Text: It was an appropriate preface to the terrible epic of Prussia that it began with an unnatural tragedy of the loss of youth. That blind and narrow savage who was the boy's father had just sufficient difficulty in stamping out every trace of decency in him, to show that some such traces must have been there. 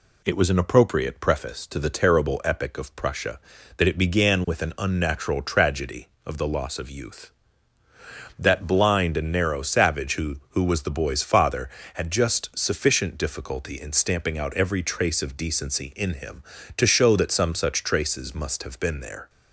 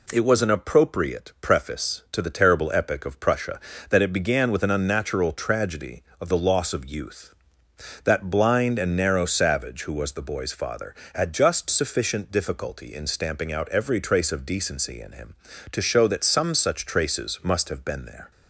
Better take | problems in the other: second | says "who" twice; at 10.4 s

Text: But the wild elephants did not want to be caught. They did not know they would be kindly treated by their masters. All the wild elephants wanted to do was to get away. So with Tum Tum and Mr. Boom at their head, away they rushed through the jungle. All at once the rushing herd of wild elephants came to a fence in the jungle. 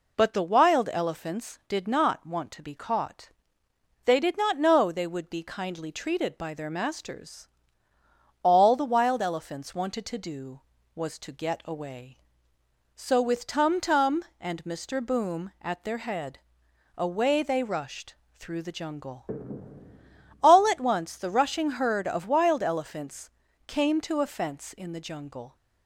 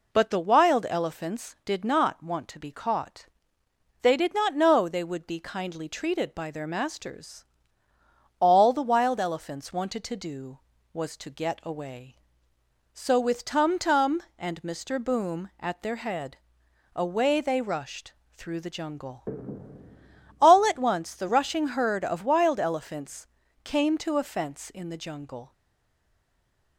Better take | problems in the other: first | pauses between "rushed" and "through"; slight; at 18.1 s; 0.24 s long; slight in the first // pauses between "elephants" and "came"; slight; at 23.2 s; 0.34 s long; slight in the first // stays silent after the last word; noticeable; from 25.5 s on; 1.2 s long

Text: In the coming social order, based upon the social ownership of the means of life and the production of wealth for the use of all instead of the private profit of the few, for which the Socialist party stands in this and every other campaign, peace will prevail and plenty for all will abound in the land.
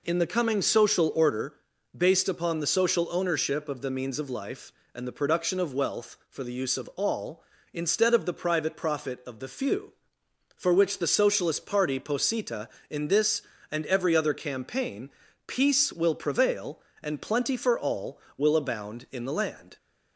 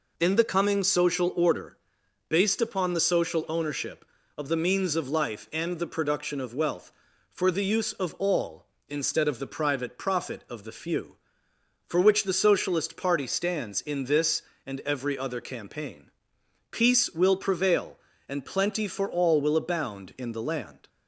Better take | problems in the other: second | says "posita" for "stands"; at 12.0 s

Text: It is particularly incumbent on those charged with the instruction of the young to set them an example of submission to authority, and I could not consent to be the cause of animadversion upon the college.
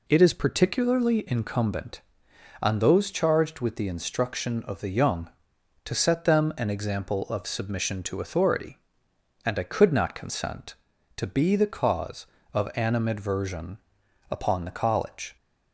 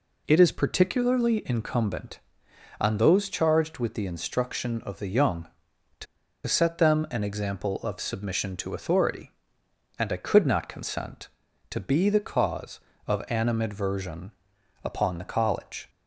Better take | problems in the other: first | pauses between "to" and "set"; at 6.0 s; 0.41 s long // pauses between "animadversion" and "upon"; noticeable; at 14.3 s; 0.52 s long; noticeable in the first

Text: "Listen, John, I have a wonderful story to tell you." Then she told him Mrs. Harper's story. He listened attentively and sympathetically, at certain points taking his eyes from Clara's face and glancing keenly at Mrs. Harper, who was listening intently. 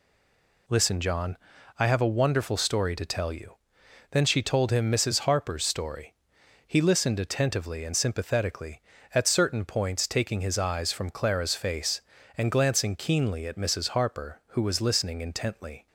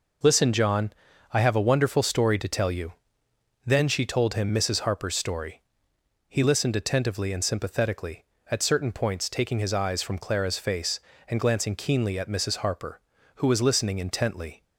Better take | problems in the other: second | stays silent before the first word; slight; until 0.6 s; 0.6 s long

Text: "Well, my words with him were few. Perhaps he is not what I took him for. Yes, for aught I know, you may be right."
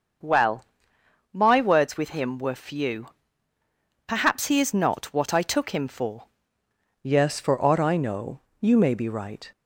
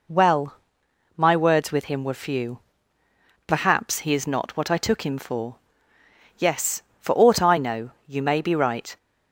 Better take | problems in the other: second | starts louder than the rest; until 1.9 s; 6.5 dB // changes voice at "Yes"; from 7.0 s on; 2.5 s long

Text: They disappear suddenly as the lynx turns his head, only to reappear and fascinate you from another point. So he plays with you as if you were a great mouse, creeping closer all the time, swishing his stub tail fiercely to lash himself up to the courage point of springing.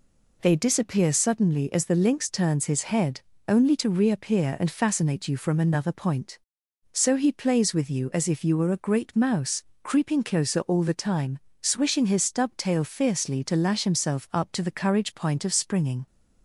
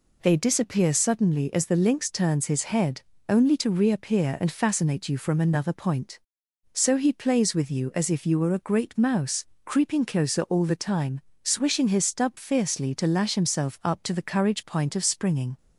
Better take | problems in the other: first | skips "tail"; at 12.3 s

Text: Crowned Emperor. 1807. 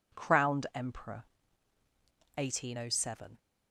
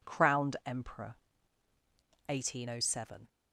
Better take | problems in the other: neither | none

